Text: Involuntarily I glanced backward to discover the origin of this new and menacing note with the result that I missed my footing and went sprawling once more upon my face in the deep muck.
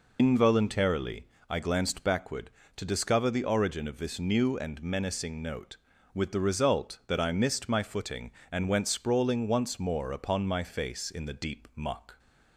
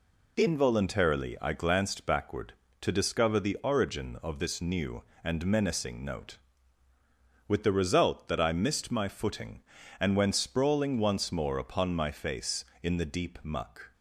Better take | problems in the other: second | loses the start of "Involuntarily"; at 0.1 s; 100 ms // pauses between "Involuntarily" and "I"; slight; at 1.2 s; 0.22 s long

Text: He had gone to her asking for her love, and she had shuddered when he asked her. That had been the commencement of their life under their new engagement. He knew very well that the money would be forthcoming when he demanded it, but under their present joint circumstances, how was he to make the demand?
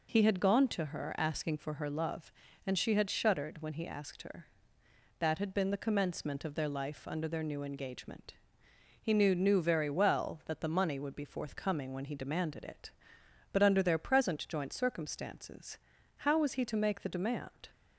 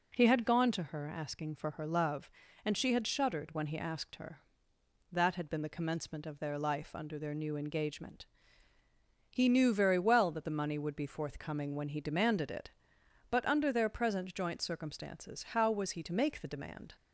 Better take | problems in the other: second | says "knew" twice; at 9.3 s

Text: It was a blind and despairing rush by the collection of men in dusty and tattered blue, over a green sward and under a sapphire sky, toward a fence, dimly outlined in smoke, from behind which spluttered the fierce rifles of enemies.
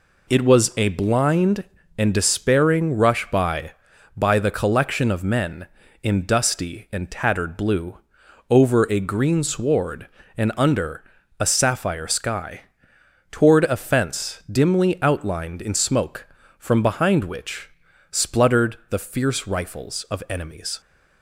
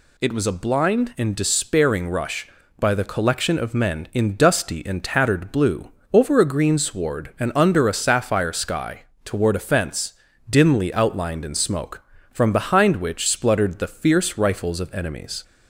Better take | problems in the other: second | says "by" twice; at 4.1 s // pauses between "under" and "a"; at 11.0 s; 0.38 s long // pauses between "which" and "spluttered"; at 17.7 s; 0.40 s long

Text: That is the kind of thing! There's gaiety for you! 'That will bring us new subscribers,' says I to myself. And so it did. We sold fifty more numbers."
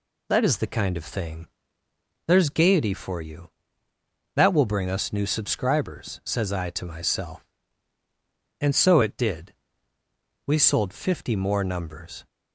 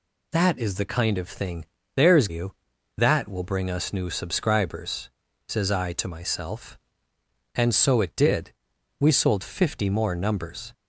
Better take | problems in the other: first | skips "gaiety for"; at 2.2 s

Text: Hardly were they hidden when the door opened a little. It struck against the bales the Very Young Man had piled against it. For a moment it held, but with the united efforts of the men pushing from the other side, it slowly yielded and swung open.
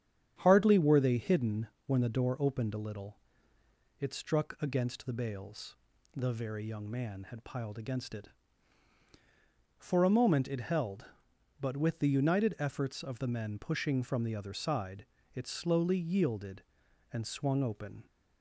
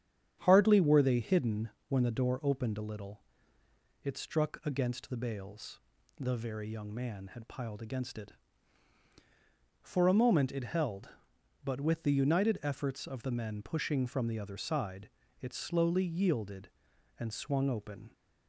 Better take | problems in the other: neither | starts louder than the rest; strong; the same in both // pauses between "hidden" and "when"; slight; the same in both // pauses between "bales" and "the"; the same in both

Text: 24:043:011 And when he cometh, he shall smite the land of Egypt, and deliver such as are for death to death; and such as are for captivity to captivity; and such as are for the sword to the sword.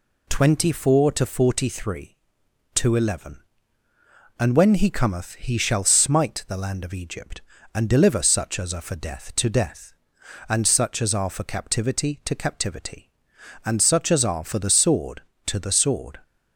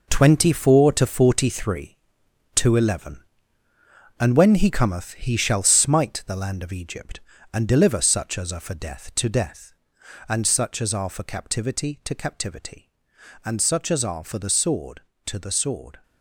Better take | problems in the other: first | gets quieter; strong; throughout; 9.5 dB

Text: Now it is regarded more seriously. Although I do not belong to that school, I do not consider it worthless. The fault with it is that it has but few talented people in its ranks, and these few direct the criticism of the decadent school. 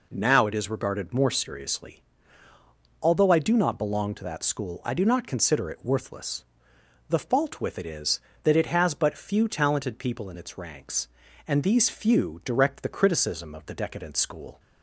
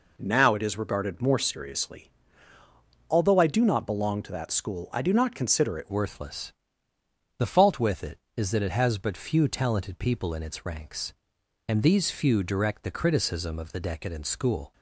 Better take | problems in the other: first | changes voice at "worthless"; from 5.8 s on; 8.9 s long

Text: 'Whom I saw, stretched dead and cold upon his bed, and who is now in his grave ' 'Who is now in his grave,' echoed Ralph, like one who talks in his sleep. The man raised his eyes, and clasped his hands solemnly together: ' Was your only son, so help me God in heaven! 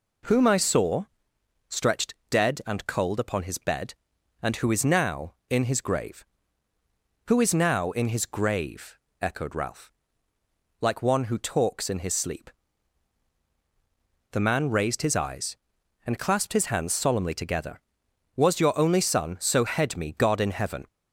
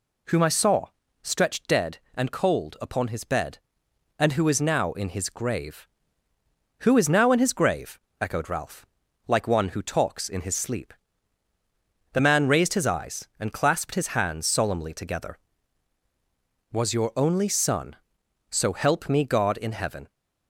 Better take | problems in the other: second | pauses between "stretched" and "dead"; slight; at 2.1 s; 0.16 s long // says "head" for "help"; at 19.6 s

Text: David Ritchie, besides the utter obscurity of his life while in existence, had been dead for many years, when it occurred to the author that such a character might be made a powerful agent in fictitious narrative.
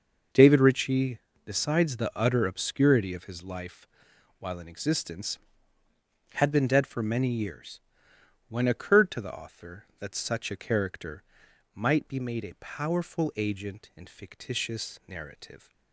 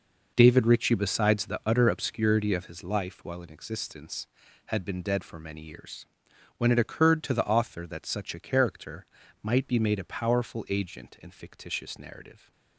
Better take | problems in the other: second | pauses between "life" and "while"; noticeable; at 3.8 s; 0.54 s long // skips "it"; at 8.6 s // pauses between "character" and "might"; noticeable; at 11.2 s; 0.52 s long; also in the second

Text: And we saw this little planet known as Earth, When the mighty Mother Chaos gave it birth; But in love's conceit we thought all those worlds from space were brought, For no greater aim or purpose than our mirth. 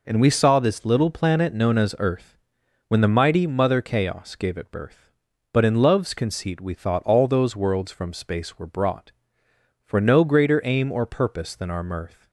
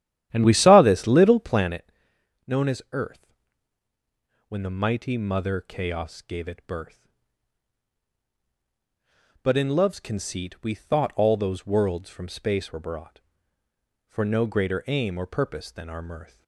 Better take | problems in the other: first | starts louder than the rest; strong; until 1.8 s; 11.5 dB // pauses between "planet" and "known"; noticeable; at 1.9 s; 0.56 s long

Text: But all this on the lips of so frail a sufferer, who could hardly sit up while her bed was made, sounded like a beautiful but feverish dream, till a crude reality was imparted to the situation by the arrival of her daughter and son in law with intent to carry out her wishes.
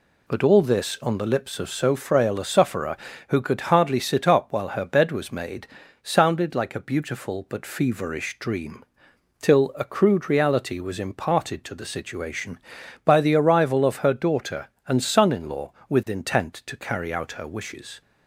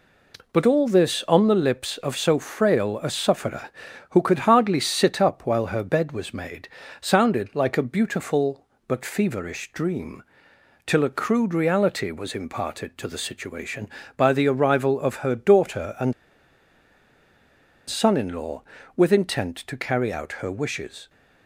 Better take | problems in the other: first | pauses between "and" and "son"; strong; at 16.1 s; 1.7 s long

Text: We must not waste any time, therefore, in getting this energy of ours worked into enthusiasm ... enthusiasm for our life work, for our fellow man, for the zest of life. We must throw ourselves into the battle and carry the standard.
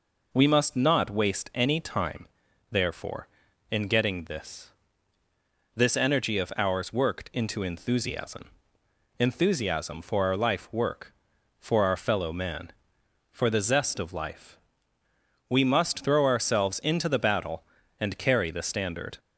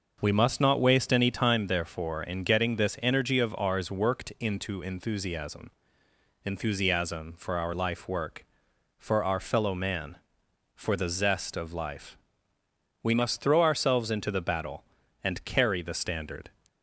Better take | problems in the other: second | says "this" twice; at 5.7 s

